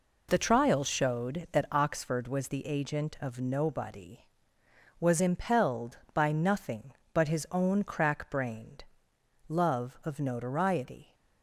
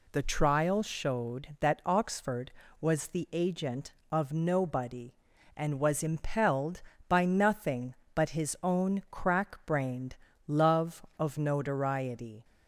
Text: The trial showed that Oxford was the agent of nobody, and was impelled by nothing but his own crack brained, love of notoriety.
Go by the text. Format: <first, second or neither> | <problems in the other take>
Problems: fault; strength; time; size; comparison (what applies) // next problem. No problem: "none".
second | skips "and"; at 4.5 s